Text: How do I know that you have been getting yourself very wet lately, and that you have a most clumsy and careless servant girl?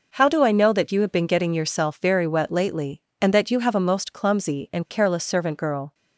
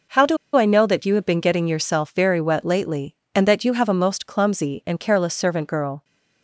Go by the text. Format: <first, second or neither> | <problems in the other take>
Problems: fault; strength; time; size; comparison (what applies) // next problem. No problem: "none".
first | pauses between "do" and "I"; slight; at 0.3 s; 0.19 s long